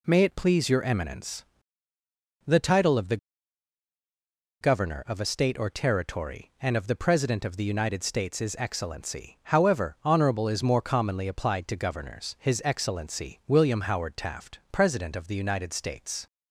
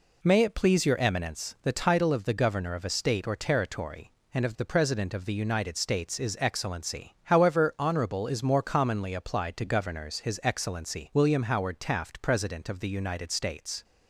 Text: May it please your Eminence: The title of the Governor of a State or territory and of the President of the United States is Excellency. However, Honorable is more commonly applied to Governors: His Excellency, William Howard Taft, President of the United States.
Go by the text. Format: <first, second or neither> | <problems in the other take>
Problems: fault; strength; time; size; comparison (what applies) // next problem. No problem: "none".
second | pauses between "the" and "Governor"; strong; at 3.1 s; 1.4 s long